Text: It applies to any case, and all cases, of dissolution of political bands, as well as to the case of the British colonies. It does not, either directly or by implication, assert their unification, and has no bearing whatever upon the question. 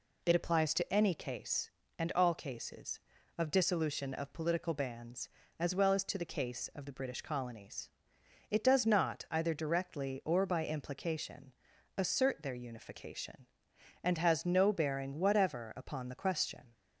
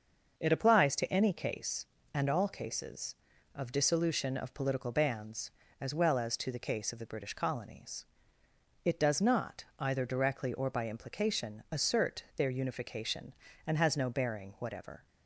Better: first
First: none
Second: starts louder than the rest; until 1.4 s; 6 dB // stops before "upon the question"; at 15.0 s

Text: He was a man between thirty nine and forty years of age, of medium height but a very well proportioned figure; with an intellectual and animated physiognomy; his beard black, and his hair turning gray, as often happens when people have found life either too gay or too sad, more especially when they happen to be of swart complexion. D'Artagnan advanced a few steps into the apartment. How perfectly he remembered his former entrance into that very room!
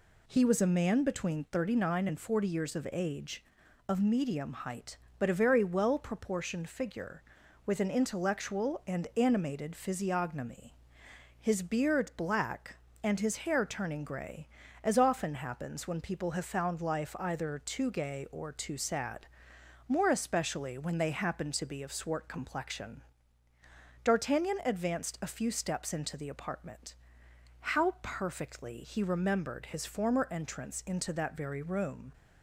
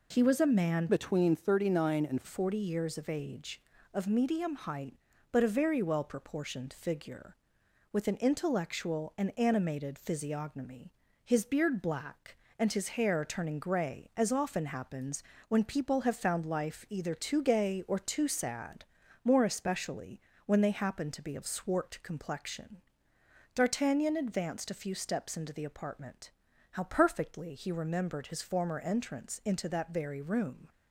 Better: first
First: none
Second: changes voice from "between" to "and"; from 0.8 to 2.2 s; 1.4 s long // pauses between "happens" and "when"; slight; at 15.2 s; 0.24 s long // pauses between "especially" and "when"; slight; at 20.1 s; 0.26 s long

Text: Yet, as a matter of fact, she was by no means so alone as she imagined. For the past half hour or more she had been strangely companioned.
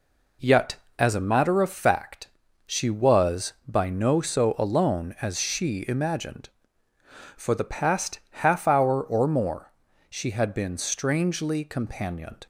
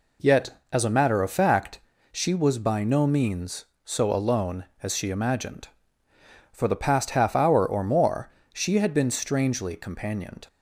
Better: second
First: skips "means"; at 4.2 s // pauses between "more" and "she"; slight; at 9.7 s; 0.36 s long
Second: pauses between "more" and "she"; slight; at 8.2 s; 0.24 s long

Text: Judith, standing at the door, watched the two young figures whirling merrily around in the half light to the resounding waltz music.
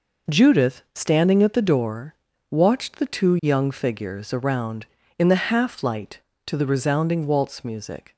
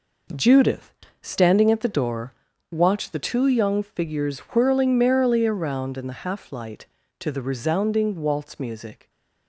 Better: second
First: skips "whirling merrily"; at 4.3 s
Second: none

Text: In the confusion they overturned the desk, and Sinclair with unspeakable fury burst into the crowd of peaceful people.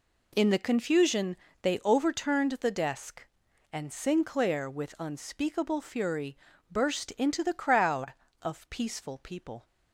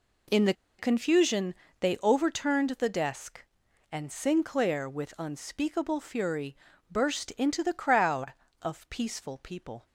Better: first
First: pauses between "confusion" and "they"; slight; at 1.3 s; 0.26 s long // pauses between "fury" and "burst"; slight; at 6.3 s; 0.31 s long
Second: pauses between "the" and "confusion"; slight; at 0.5 s; 0.25 s long // pauses between "confusion" and "they"; slight; at 1.5 s; 0.26 s long // pauses between "fury" and "burst"; slight; at 6.5 s; 0.32 s long

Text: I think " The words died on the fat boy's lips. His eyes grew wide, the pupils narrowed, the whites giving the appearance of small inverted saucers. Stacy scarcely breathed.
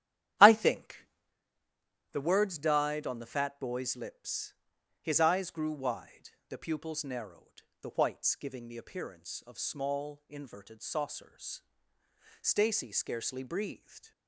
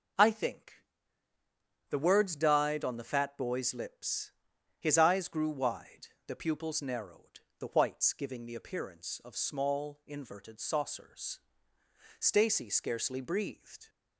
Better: second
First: starts louder than the rest; strong; until 1.4 s; 11.5 dB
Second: none

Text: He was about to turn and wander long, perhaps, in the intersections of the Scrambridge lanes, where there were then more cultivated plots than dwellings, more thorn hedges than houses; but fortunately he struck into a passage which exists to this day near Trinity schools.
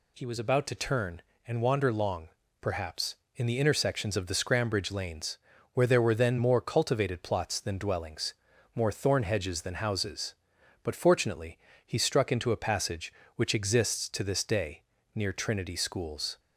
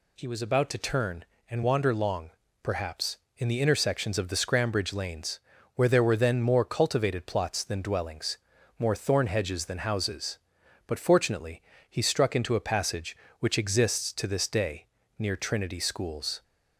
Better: neither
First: pauses between "fortunately" and "he"; slight; at 11.5 s; 0.28 s long // pauses between "day" and "near"; slight; at 14.8 s; 0.32 s long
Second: pauses between "fortunately" and "he"; slight; at 11.6 s; 0.28 s long // pauses between "day" and "near"; slight; at 14.8 s; 0.32 s long

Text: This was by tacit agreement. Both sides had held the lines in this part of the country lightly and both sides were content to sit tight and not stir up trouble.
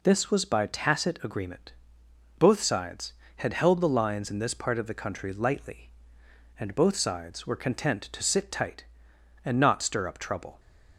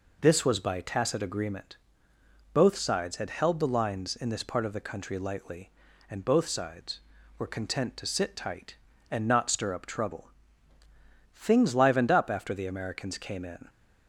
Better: first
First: none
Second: goes on to say "Things livened up after the Americans came in"; strong; from 11.3 s on; 2.3 s long

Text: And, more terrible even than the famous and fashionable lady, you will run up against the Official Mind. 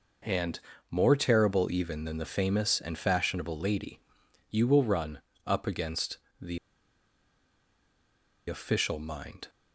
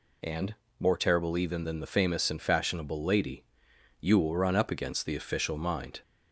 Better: second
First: pauses between "run" and "up"; slight; at 5.1 s; 0.26 s long // pauses between "against" and "the"; slight; at 6.1 s; 0.22 s long // pauses between "the" and "Official"; strong; at 6.5 s; 1.9 s long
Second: none

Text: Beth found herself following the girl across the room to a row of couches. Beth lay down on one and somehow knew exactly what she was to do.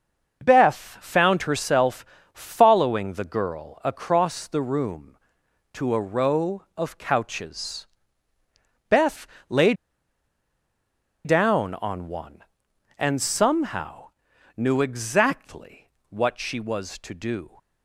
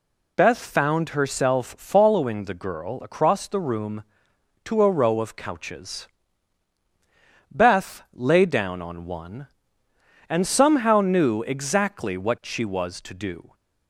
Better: second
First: starts louder than the rest; until 1.4 s; 6 dB // pauses between "herself" and "following"; slight; at 2.0 s; 0.28 s long // pauses between "Beth" and "lay"; slight; at 9.2 s; 0.22 s long // pauses between "lay" and "down"; strong; at 9.7 s; 1.5 s long // pauses between "somehow" and "knew"; noticeable; at 14.0 s; 0.48 s long // pauses between "exactly" and "what"; slight; at 15.8 s; 0.20 s long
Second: none

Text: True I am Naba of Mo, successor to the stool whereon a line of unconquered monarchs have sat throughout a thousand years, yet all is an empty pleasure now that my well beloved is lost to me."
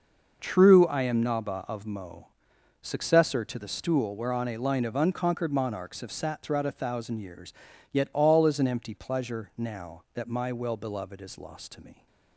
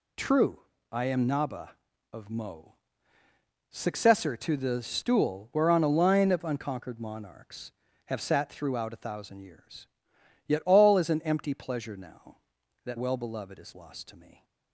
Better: first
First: none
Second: pauses between "True" and "I"; slight; at 0.6 s; 0.30 s long // skips "my"; at 12.9 s

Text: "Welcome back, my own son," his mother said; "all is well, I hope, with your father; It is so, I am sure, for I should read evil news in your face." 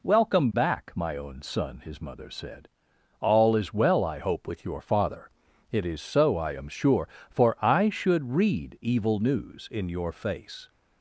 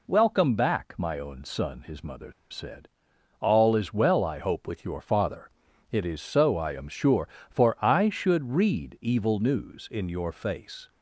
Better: first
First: none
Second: pauses between "mother" and "said"; slight; at 2.3 s; 0.19 s long

